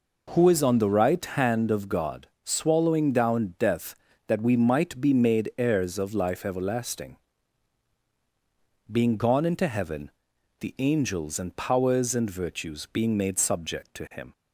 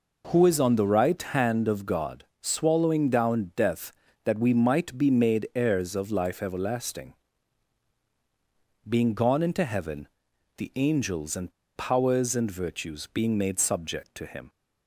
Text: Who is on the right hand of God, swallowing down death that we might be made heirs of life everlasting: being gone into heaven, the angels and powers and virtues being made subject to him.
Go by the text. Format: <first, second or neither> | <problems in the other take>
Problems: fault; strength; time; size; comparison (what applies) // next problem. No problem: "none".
first | pauses between "and" and "powers"; slight; at 11.5 s; 0.25 s long